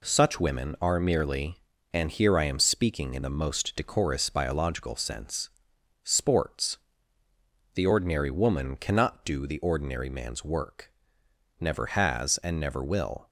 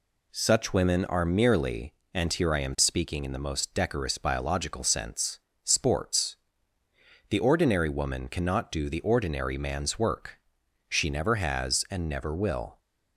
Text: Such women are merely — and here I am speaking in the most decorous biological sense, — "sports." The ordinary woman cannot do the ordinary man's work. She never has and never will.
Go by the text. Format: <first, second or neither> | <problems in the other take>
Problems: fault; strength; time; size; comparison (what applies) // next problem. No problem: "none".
second | skips "She"; at 11.2 s